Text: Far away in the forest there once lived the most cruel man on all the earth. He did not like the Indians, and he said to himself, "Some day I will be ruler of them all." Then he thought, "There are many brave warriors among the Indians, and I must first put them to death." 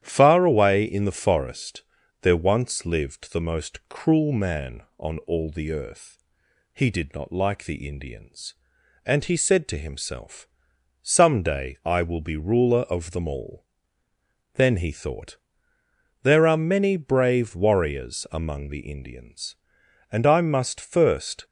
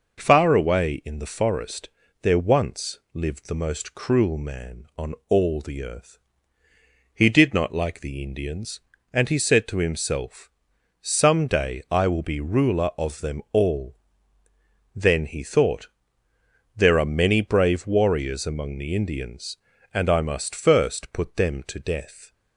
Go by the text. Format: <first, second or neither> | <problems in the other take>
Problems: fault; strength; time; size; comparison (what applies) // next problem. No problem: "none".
second | starts louder than the rest; strong; until 1.0 s; 10 dB // pauses between "forest" and "there"; at 1.8 s; 0.38 s long; slight in the second // stops before "put them to death"; at 21.4 s